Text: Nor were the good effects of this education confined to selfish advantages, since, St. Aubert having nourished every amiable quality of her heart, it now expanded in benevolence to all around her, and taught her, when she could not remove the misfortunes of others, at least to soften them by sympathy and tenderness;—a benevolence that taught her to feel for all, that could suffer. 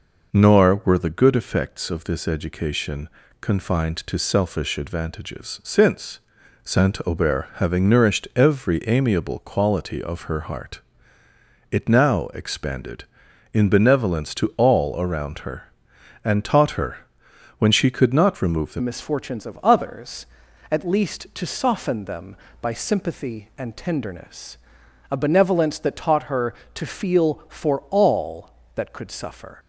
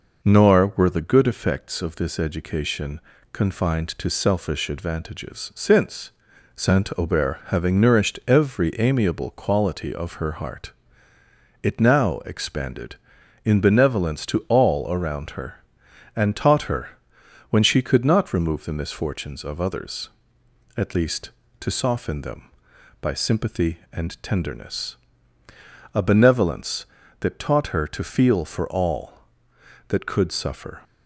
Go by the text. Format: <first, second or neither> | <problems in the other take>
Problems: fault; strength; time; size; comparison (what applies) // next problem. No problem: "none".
second | pauses between "education" and "confined"; slight; at 3.0 s; 0.32 s long; slight in the second // changes voice at "misfortunes"; from 18.8 s on; 10.7 s long